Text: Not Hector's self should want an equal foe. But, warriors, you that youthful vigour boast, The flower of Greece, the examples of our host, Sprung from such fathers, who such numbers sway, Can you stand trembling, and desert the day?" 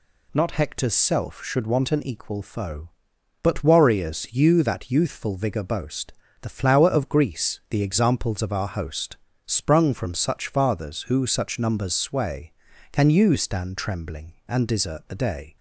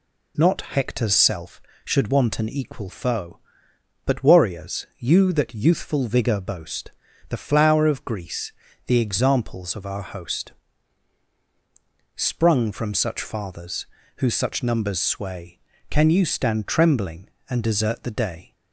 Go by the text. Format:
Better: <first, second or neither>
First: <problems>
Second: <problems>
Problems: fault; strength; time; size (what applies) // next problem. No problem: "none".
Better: neither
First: none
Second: none